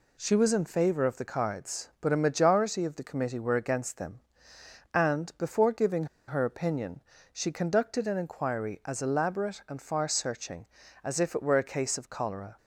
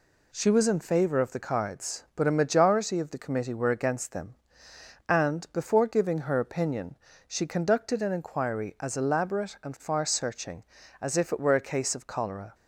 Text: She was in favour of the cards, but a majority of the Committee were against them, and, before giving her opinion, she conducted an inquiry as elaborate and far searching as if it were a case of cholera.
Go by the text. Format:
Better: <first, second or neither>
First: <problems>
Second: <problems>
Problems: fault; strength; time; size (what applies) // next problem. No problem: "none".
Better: second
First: pauses between "giving" and "her"; slight; at 6.0 s; 0.22 s long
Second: none